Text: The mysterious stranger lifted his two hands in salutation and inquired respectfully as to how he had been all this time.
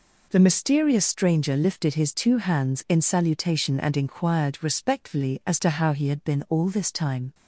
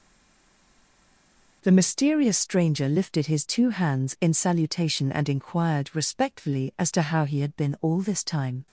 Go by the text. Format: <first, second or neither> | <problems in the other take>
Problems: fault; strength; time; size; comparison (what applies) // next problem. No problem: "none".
first | stays silent before the first word; noticeable; until 1.6 s; 1.6 s long